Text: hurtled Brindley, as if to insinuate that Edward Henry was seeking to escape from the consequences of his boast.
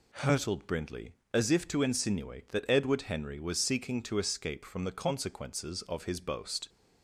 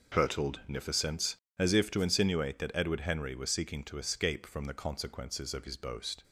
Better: first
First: none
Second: says "Nificence" for "Brindley"; at 0.6 s

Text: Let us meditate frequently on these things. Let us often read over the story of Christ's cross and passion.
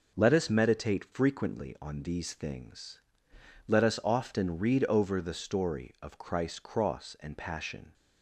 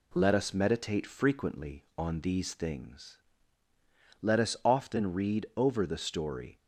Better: first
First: none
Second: stops before "of Christ's cross and passion"; at 6.5 s

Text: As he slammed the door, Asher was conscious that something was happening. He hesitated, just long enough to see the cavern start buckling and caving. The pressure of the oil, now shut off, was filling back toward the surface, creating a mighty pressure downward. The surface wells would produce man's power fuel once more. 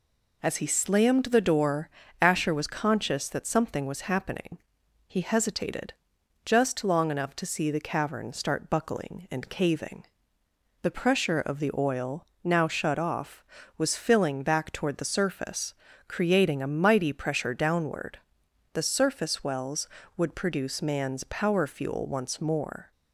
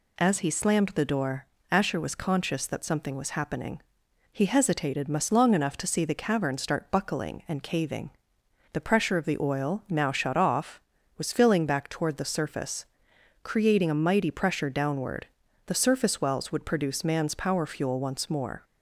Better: first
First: none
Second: says "must" for "just"; at 5.0 s

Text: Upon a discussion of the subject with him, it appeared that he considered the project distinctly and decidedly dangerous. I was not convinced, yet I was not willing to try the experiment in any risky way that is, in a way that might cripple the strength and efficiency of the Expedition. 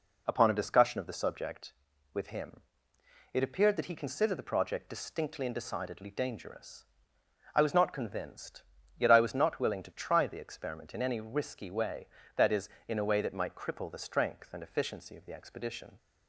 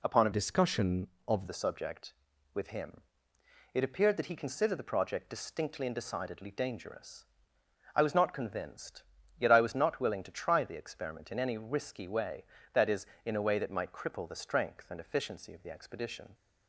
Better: first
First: none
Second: changes voice from "discussion" to "of"; from 0.3 to 1.4 s; 1.1 s long

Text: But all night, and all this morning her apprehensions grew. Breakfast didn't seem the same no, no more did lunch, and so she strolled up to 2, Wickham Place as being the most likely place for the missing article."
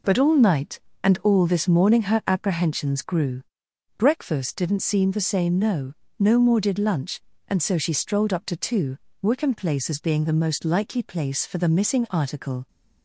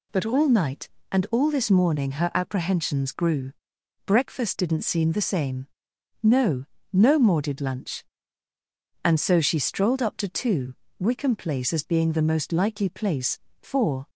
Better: first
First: none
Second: pauses between "same" and "no"; noticeable; at 5.6 s; 0.54 s long // stops before "the missing article"; at 14.0 s

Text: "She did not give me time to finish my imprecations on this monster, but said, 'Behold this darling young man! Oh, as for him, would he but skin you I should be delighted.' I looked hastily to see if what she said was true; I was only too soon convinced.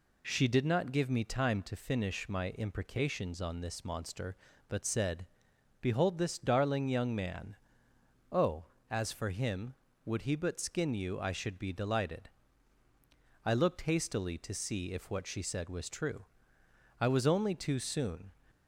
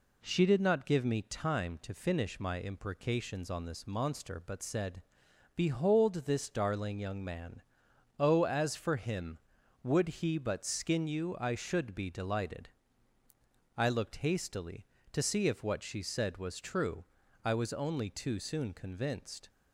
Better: second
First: stops before "convinced"; at 18.4 s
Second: none

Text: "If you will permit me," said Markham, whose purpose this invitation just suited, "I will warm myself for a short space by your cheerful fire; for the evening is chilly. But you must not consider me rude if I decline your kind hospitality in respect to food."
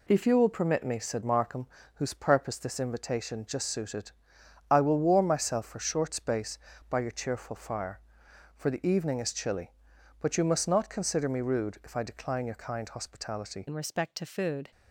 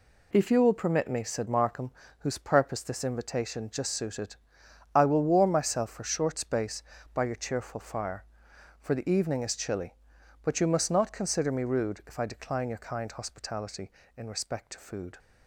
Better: second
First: changes voice at "in"; from 13.6 s on; 1.1 s long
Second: none

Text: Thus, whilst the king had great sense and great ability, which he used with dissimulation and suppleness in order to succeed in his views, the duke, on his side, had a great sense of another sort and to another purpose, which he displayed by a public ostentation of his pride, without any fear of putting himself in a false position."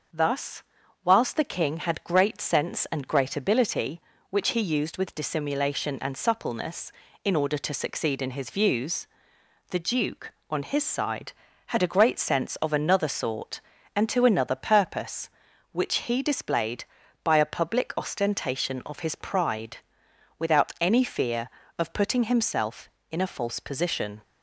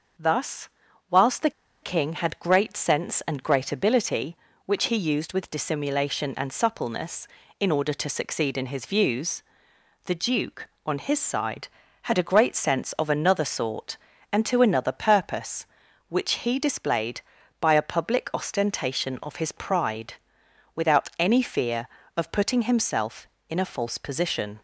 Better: first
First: starts louder than the rest; until 1.5 s; 6 dB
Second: starts louder than the rest; until 1.9 s; 6 dB // pauses between "the" and "king"; slight; at 1.5 s; 0.31 s long

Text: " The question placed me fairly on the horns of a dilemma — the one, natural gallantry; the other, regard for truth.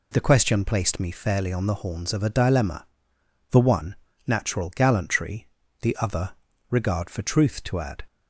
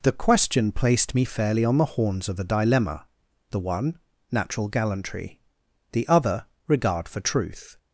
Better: second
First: goes on to say "To add"; slight; from 7.6 s on; 0.42 s long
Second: none

